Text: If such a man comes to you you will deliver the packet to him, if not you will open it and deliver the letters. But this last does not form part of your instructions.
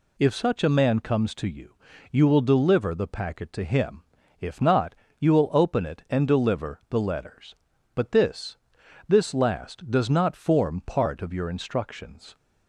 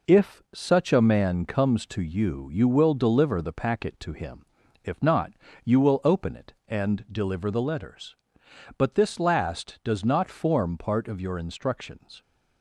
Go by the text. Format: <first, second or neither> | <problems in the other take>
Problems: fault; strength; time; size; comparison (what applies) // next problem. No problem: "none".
second | pauses between "you" and "you"; slight; at 1.7 s; 0.36 s long // pauses between "not" and "you"; slight; at 4.9 s; 0.24 s long; slight in the second // says "this" twice; at 9.0 s